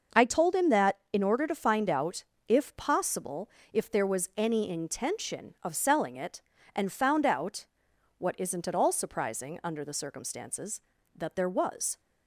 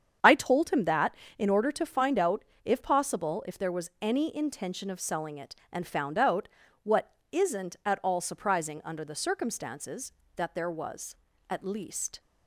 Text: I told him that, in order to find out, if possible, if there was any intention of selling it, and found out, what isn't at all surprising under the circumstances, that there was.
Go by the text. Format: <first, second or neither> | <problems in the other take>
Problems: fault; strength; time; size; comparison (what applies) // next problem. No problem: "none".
first | starts louder than the rest; strong; until 1.4 s; 8 dB // pauses between "what" and "isn't"; slight; at 7.1 s; 0.20 s long // goes on to say "At least"; noticeable; from 11.4 s on; 0.70 s long